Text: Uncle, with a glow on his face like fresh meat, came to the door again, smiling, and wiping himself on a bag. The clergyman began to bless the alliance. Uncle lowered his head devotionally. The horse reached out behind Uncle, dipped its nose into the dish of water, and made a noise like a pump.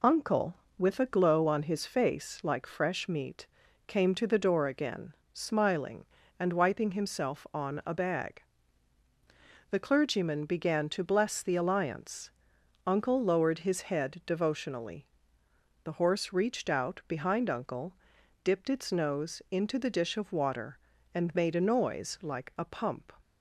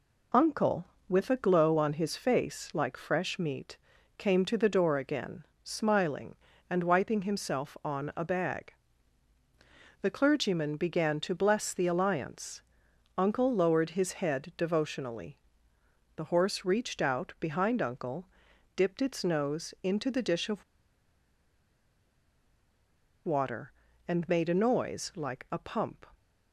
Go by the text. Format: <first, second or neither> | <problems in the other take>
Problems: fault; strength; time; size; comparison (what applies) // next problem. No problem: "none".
first | pauses between "of" and "water"; strong; at 20.6 s; 2.6 s long